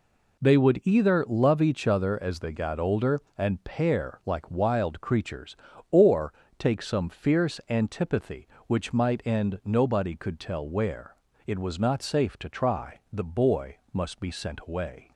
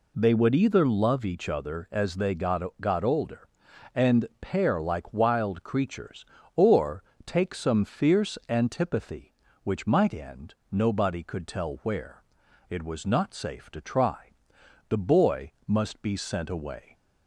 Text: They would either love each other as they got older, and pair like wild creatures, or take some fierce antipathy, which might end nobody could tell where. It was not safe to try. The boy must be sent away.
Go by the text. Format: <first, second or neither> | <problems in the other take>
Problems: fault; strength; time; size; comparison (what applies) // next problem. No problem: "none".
first | says "got" twice; at 2.7 s // pauses between "or" and "take"; slight; at 7.0 s; 0.22 s long; slight in the first // pauses between "end" and "nobody"; slight; at 10.5 s; 0.18 s long // pauses between "boy" and "must"; slight; at 15.5 s; 0.16 s long; slight in the first